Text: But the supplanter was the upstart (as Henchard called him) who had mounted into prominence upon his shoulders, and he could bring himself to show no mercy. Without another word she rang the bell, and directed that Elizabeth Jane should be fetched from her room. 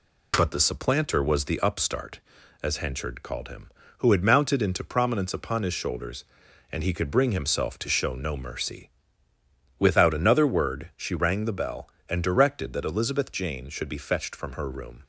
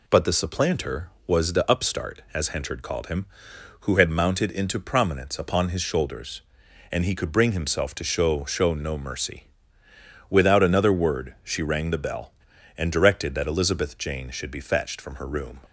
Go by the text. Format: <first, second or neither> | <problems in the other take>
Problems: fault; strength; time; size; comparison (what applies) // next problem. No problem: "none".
first | says "show" twice; at 8.4 s